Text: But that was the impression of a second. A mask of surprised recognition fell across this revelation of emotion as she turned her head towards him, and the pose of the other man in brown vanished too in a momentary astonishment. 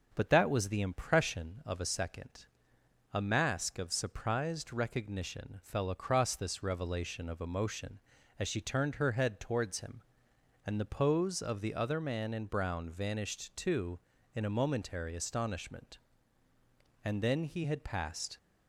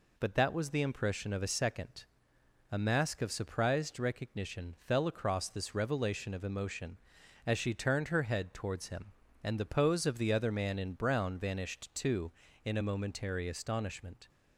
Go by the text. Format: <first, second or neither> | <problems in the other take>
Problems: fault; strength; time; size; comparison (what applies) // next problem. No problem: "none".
second | goes on to say "And then he had passed"; from 17.0 s on; 1.3 s long